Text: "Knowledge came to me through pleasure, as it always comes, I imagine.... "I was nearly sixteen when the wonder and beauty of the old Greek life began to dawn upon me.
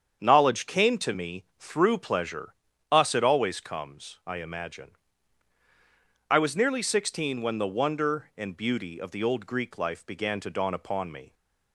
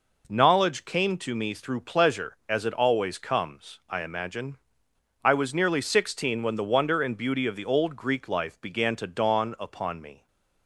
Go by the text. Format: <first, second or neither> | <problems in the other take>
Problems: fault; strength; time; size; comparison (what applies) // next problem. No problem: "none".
second | starts louder than the rest; strong; until 1.2 s; 8 dB // says "us" for "as"; at 2.9 s